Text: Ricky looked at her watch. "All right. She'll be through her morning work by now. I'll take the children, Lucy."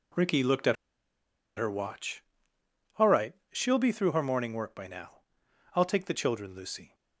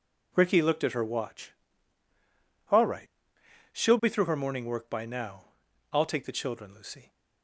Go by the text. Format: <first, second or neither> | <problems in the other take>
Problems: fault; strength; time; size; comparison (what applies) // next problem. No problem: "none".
second | pauses between "at" and "her"; noticeable; at 0.7 s; 0.81 s long